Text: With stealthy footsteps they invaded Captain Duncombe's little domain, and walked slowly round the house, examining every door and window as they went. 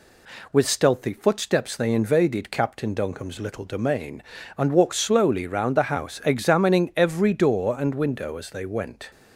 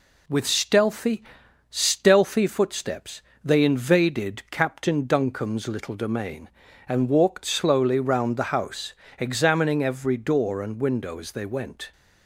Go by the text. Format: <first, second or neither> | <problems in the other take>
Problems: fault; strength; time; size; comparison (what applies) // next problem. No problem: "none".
first | says "stealthy" twice; at 1.6 s // pauses between "footsteps" and "they"; slight; at 3.2 s; 0.22 s long